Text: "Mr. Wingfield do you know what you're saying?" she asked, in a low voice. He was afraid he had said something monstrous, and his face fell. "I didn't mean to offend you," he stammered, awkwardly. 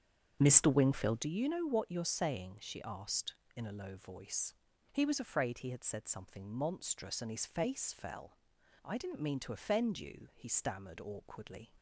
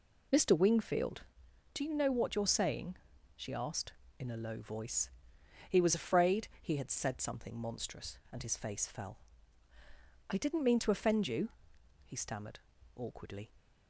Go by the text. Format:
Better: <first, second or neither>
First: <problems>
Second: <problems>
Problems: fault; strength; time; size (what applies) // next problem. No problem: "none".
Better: second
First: starts louder than the rest; strong; until 1.3 s; 7.5 dB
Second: none